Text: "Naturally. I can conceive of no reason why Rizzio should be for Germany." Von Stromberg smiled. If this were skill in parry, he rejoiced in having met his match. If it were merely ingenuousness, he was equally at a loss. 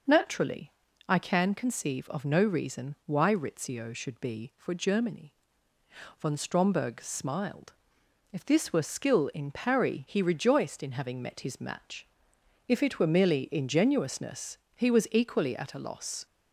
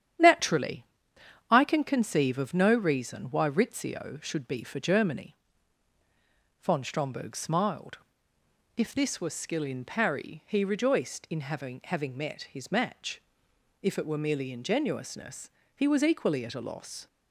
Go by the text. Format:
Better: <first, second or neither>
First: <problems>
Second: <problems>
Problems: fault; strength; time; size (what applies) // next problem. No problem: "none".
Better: first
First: none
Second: starts louder than the rest; strong; until 1.8 s; 10 dB // says "having" twice; at 11.8 s